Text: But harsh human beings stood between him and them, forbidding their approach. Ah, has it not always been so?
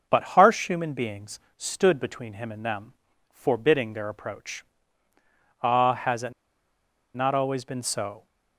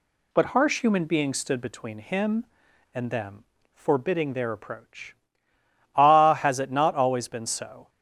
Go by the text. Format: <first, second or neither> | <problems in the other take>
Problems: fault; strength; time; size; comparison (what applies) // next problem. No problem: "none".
second | pauses between "beings" and "stood"; slight; at 1.3 s; 0.18 s long // pauses between "it" and "not"; noticeable; at 6.3 s; 0.81 s long